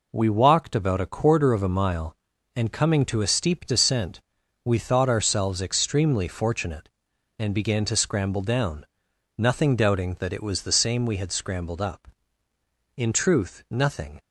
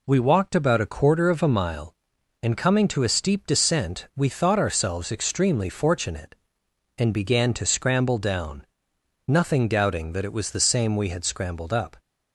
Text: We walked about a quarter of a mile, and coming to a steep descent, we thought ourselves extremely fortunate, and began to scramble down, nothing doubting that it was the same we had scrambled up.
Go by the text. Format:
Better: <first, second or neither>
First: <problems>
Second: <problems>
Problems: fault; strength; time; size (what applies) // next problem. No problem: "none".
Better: second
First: goes on to say "In truth nothing"; noticeable; from 12.9 s on; 1.2 s long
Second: none